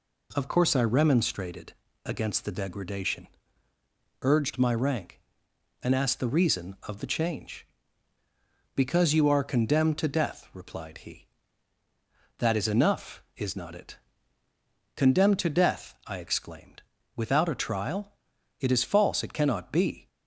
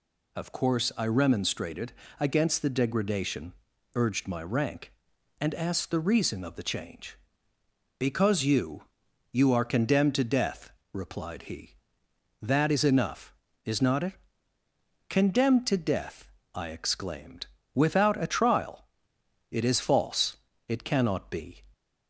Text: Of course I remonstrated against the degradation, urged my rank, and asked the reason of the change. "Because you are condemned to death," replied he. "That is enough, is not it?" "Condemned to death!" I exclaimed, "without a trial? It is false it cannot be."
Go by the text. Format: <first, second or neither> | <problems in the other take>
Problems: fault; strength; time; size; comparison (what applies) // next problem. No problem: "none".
first | pauses between "remonstrated" and "against"; slight; at 1.9 s; 0.26 s long; slight in the first // says "you" twice; at 9.3 s // pauses between "false" and "it"; slight; at 20.3 s; 0.28 s long